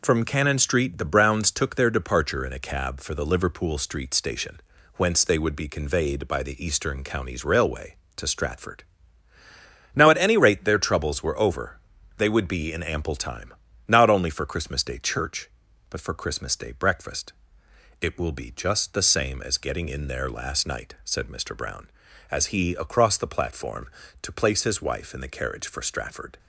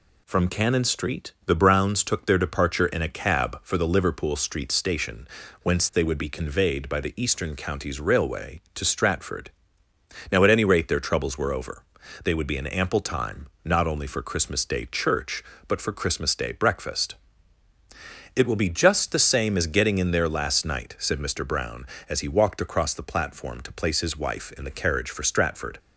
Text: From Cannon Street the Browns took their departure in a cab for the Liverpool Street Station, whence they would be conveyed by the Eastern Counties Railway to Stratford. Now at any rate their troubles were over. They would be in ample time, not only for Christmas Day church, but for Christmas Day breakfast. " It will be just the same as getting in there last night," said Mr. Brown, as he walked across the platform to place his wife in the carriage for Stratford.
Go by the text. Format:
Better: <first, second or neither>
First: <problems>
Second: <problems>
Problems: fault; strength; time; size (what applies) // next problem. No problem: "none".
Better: second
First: skips "walked"; at 22.7 s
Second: none